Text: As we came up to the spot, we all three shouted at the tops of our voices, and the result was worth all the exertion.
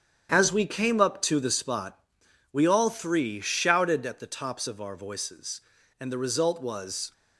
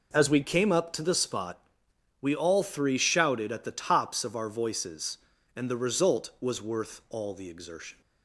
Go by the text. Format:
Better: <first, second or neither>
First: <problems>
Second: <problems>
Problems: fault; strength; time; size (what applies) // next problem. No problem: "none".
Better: second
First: starts louder than the rest; strong; until 1.3 s; 8.5 dB // stops before "worth all the exertion"; at 7.1 s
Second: none